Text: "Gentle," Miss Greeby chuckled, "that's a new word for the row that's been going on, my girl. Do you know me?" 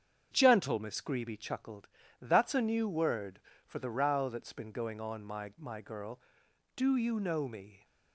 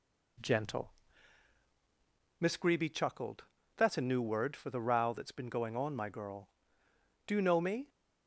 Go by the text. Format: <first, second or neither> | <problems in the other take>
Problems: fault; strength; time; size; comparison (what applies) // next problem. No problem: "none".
second | starts louder than the rest; strong; until 1.3 s; 7.5 dB // says "my" twice; at 5.5 s